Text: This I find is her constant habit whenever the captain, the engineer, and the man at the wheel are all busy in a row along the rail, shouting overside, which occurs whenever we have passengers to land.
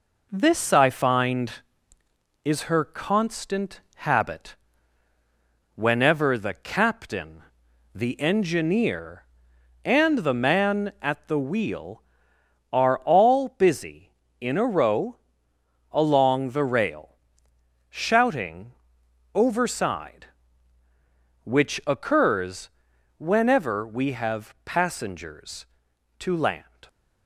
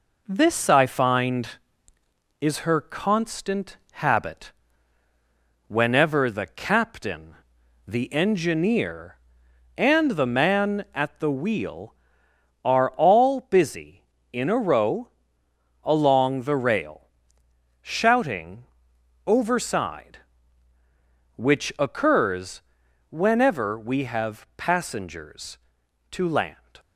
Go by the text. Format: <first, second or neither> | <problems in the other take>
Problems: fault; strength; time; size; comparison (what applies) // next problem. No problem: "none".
neither | pauses between "constant" and "habit"; slight; the same in both // pauses between "habit" and "whenever"; the same in both // pauses between "row" and "along"; noticeable; the same in both // pauses between "shouting" and "overside"; noticeable; the same in both // pauses between "occurs" and "whenever"; noticeable; the same in both